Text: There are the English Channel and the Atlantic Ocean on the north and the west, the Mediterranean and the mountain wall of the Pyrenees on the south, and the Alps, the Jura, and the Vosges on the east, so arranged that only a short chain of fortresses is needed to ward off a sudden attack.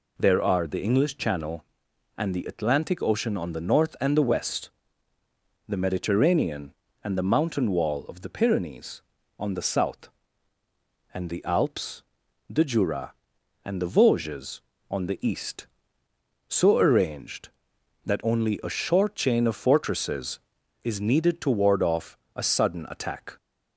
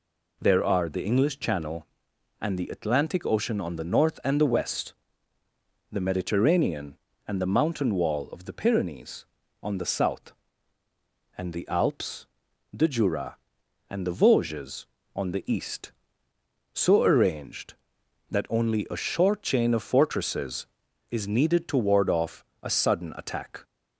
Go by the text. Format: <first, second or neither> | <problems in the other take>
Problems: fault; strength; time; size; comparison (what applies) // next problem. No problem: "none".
neither | pauses between "off" and "a"; slight; the same in both